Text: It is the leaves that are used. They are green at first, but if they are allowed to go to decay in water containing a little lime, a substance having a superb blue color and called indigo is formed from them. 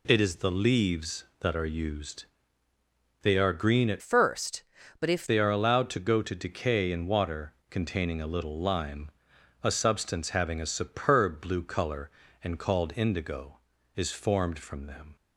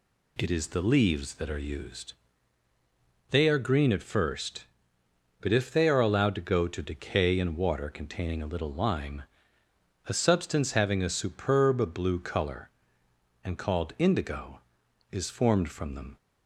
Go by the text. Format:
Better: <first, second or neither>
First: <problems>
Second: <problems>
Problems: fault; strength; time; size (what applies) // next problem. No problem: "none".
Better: second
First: changes voice from "first" to "if"; from 4.0 to 5.2 s; 1.2 s long // pauses between "water" and "containing"; slight; at 7.5 s; 0.18 s long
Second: none